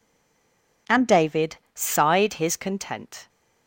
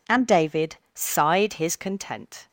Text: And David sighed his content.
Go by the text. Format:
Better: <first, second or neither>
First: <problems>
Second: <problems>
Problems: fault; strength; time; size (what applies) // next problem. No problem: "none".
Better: second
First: stays silent before the first word; slight; until 0.8 s; 0.8 s long // pauses between "David" and "sighed"; slight; at 1.5 s; 0.16 s long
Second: pauses between "David" and "sighed"; slight; at 0.7 s; 0.16 s long